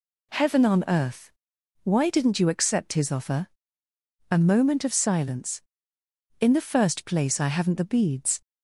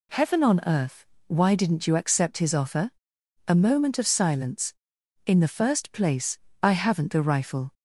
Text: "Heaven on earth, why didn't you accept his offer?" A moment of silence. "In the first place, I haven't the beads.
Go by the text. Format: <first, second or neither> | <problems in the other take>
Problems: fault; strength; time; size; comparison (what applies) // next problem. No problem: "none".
first | says "rifle" for "beads"; at 7.2 s